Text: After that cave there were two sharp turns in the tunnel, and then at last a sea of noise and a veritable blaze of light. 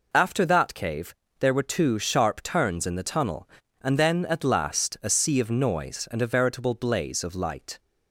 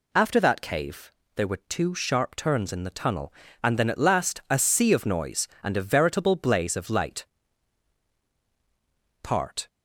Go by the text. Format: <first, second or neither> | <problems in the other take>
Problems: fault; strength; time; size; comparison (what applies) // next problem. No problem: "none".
first | pauses between "cave" and "there"; slight; at 1.1 s; 0.24 s long; slight in the first // goes on to say "Part"; slight; from 9.2 s on; 0.46 s long